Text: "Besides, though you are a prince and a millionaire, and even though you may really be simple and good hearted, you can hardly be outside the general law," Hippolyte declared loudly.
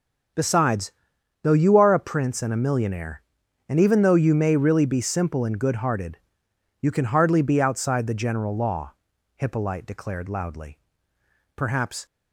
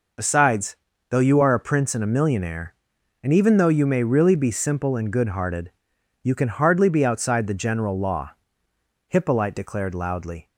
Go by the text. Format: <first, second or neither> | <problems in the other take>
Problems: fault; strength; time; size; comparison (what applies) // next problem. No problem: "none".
second | starts louder than the rest; until 1.8 s; 6.5 dB // goes on to say "Perhaps"; from 11.5 s on; 0.50 s long